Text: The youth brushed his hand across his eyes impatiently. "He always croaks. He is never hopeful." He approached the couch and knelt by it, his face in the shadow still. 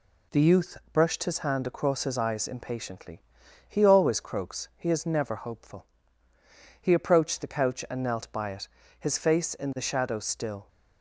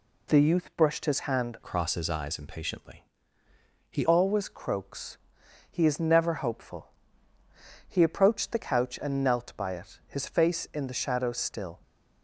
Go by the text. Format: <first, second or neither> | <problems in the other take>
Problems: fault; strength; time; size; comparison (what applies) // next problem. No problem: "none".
first | changes voice from "across" to "He"; from 1.6 to 4.0 s; 2.4 s long